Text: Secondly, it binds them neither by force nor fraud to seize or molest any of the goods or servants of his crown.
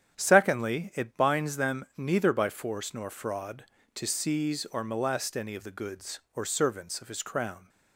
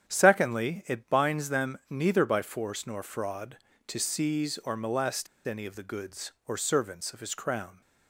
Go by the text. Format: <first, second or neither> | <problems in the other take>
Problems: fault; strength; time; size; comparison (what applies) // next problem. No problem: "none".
first | starts louder than the rest; strong; until 1.1 s; 8.5 dB; strong in the first // pauses between "molest" and "any"; slight; at 5.2 s; 0.19 s long